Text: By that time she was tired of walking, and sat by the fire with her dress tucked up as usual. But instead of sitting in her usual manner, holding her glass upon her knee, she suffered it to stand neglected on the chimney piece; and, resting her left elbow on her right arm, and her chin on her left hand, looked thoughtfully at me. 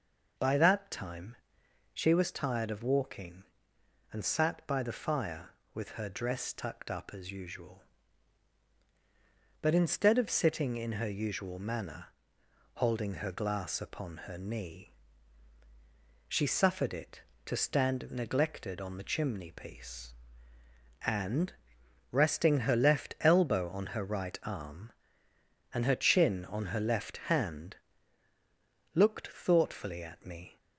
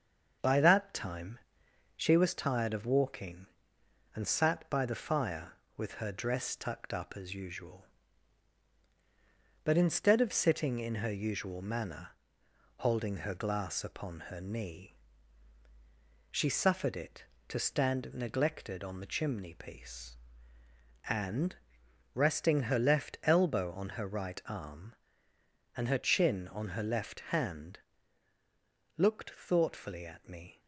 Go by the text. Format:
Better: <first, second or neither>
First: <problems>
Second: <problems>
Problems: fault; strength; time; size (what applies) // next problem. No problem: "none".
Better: first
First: pauses between "time" and "she"; noticeable; at 1.3 s; 0.56 s long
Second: gets quieter; slight; throughout; 3 dB // pauses between "time" and "she"; noticeable; at 1.3 s; 0.56 s long